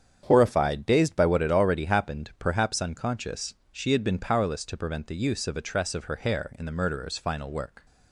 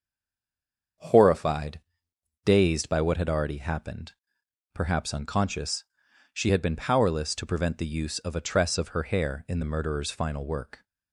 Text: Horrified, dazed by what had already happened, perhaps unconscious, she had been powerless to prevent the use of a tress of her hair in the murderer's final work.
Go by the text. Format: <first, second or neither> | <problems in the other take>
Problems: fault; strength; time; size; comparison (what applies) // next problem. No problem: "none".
first | stays silent before the first word; until 0.9 s; 0.9 s long // starts louder than the rest; strong; until 2.6 s; 7 dB; strong in the first